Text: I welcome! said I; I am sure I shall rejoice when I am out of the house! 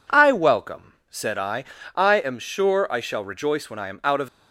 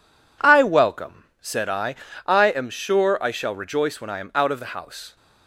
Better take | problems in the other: second | stops before "the house"; at 4.2 s

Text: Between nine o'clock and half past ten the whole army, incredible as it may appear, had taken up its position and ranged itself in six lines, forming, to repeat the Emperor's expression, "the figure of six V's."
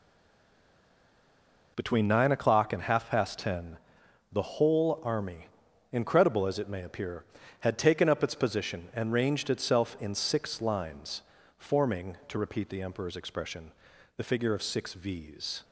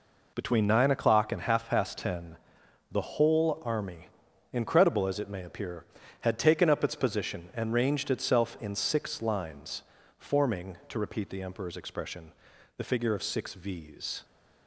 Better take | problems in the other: second | stays silent before the first word; noticeable; until 1.7 s; 1.7 s long // pauses between "ten" and "the"; noticeable; at 3.7 s; 0.54 s long; noticeable in the second

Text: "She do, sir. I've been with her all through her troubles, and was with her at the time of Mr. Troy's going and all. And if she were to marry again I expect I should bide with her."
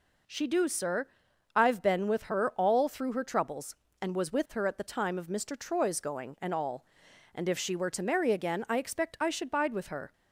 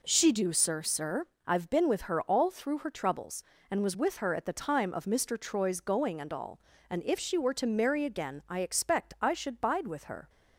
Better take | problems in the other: first | says "sir" twice; at 0.8 s

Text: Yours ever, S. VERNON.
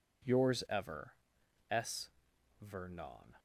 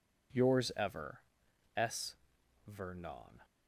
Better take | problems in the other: neither | none

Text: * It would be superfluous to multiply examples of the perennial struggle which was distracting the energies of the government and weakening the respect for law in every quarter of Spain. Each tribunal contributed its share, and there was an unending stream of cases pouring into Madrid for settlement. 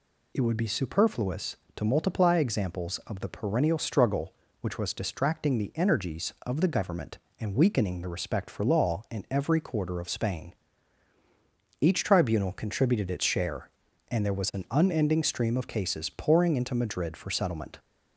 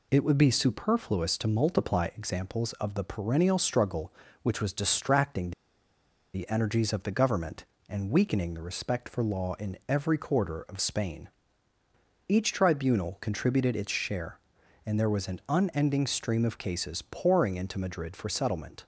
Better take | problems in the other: first | pauses between "distracting" and "the"; noticeable; at 5.5 s; 0.83 s long

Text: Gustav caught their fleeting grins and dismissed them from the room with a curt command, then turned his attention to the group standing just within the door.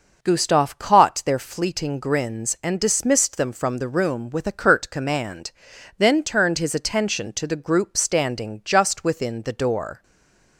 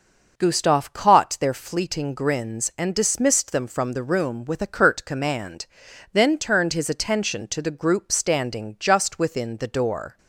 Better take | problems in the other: second | stays silent after the last word; slight; from 10.0 s on; 0.5 s long

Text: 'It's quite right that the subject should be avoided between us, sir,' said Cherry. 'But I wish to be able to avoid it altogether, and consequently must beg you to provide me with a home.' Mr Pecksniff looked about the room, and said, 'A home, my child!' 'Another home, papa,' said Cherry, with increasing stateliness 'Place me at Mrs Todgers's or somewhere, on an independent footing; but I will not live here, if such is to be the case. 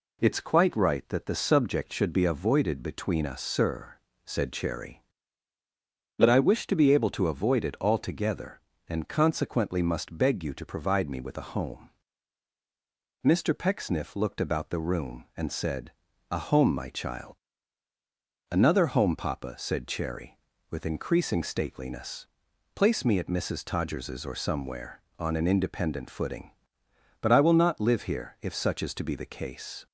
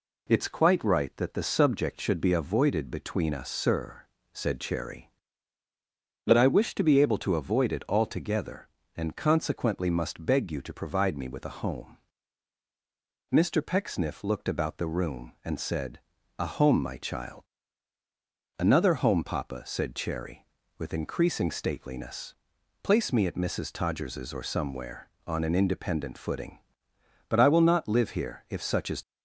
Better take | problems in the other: first | pauses between "stateliness" and "Place"; noticeable; at 22.3 s; 0.48 s long; noticeable in the first // stops before "to be the case"; at 29.0 s

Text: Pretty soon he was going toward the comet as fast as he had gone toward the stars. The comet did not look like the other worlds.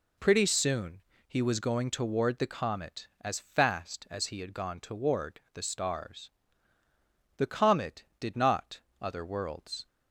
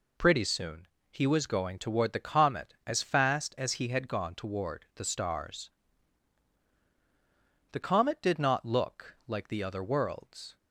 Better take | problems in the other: second | pauses between "soon" and "he"; slight; at 1.0 s; 0.28 s long; slight in the second // skips "look like the"; at 8.9 s

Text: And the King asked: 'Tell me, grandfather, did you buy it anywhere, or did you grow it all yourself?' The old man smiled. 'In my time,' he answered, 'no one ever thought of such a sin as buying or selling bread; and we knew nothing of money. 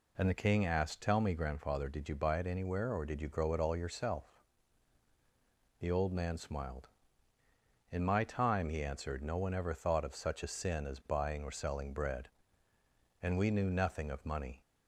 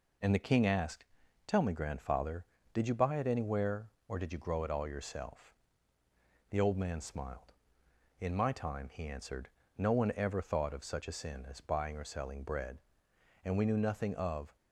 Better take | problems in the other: first | stops before "money"; at 14.5 s

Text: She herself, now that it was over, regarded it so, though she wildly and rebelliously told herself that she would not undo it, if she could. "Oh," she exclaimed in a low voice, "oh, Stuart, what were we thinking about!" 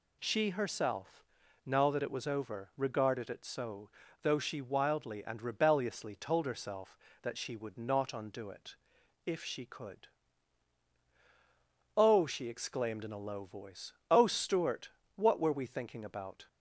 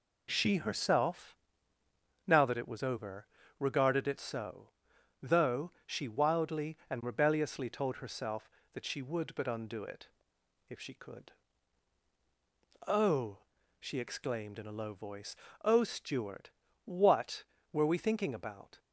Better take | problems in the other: first | pauses between "though" and "she"; slight; at 5.7 s; 0.16 s long // says "but" for "not"; at 9.3 s

